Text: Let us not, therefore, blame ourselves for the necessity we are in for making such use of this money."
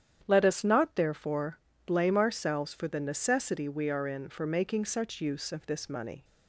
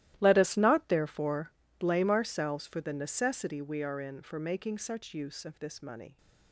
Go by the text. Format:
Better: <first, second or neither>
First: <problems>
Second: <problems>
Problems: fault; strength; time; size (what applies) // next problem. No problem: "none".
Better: first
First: starts louder than the rest; strong; until 1.2 s; 9.5 dB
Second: gets quieter; strong; throughout; 17 dB // starts louder than the rest; strong; until 1.2 s; 14.5 dB